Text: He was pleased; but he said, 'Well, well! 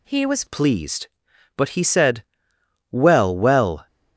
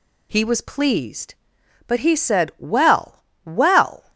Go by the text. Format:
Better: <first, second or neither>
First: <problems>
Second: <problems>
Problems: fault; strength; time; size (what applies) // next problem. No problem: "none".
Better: second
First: changes voice at "pleased"; from 0.4 s on; 3.4 s long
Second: none